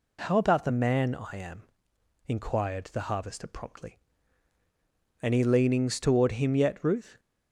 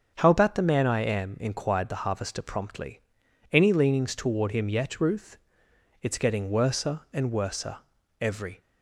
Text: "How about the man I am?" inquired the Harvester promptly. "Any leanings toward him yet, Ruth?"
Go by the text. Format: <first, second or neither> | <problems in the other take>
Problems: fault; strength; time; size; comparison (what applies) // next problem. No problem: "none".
first | starts louder than the rest; until 1.1 s; 7 dB // goes on to say "It's getting worser and worser every"; strong; from 6.0 s on; 2.5 s long